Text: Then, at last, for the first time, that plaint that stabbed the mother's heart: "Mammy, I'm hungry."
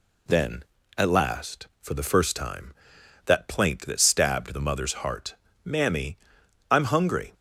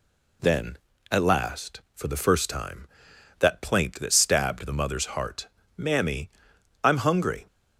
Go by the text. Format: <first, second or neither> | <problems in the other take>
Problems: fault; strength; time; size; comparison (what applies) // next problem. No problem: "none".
neither | none